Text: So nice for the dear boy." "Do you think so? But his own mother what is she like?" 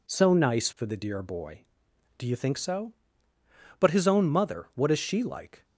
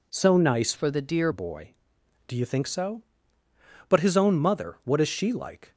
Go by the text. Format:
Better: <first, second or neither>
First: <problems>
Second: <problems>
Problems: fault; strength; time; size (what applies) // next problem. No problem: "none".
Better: first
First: none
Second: changes voice from "for" to "dear"; from 0.7 to 1.3 s; 0.6 s long